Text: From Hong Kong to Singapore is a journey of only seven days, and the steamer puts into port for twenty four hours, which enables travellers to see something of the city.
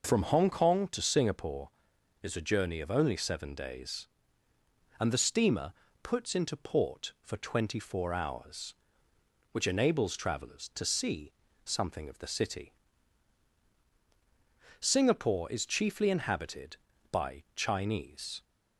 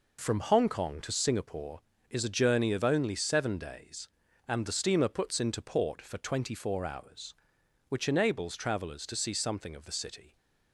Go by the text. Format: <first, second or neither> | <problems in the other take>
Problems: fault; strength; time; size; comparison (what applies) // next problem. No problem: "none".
second | pauses between "steamer" and "puts"; slight; at 5.7 s; 0.30 s long // pauses between "see" and "something"; slight; at 11.3 s; 0.32 s long // goes on to say "Singapore is chiefly inhabited by Chinese"; strong; from 14.7 s on; 3.6 s long